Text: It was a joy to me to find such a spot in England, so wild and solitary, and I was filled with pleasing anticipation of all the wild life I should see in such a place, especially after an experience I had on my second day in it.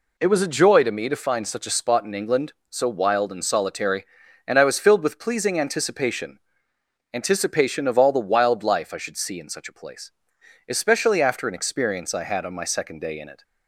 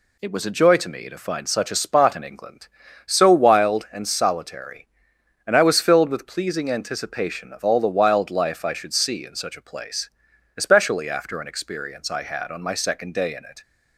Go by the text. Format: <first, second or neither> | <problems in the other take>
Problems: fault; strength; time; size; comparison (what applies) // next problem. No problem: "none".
second | says "anticipation" twice; at 7.1 s